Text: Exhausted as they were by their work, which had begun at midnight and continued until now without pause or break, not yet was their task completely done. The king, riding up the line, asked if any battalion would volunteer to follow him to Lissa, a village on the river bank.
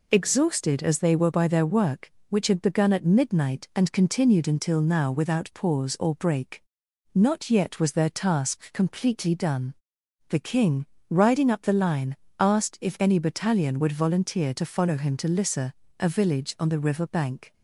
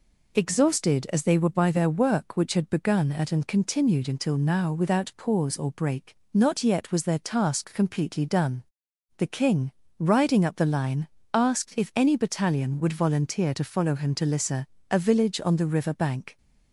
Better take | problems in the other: first | skips "midnight"; at 3.3 s

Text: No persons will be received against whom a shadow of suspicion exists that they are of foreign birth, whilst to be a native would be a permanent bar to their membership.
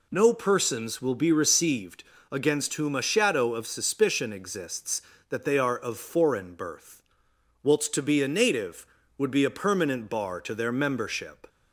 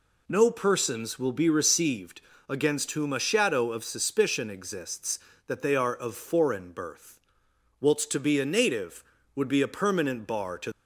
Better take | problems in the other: first | pauses between "received" and "against"; slight; at 2.1 s; 0.30 s long; slight in the first // stops before "their membership"; at 10.7 s

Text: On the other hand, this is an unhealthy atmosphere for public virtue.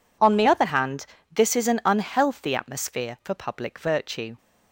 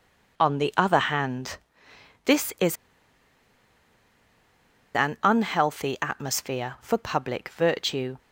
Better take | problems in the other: first | pauses between "is" and "an"; strong; at 2.7 s; 2.1 s long

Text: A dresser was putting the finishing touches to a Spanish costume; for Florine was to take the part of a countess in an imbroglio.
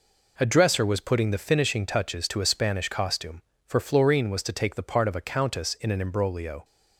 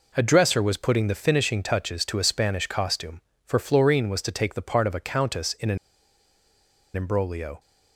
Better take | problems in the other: first | pauses between "an" and "imbroglio"; at 5.7 s; 1.1 s long

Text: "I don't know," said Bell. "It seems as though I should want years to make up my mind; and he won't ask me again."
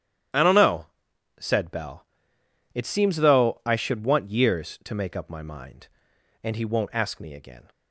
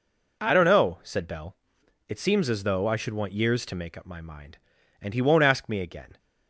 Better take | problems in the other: second | starts louder than the rest; strong; until 1.8 s; 11.5 dB // skips "as"; at 3.1 s

